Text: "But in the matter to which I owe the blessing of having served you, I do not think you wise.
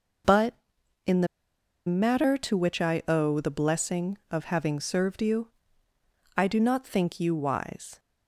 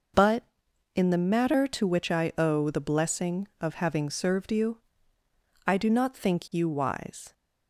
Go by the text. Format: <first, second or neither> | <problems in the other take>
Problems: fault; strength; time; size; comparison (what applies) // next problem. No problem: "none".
second | pauses between "the" and "matter"; noticeable; at 1.2 s; 0.60 s long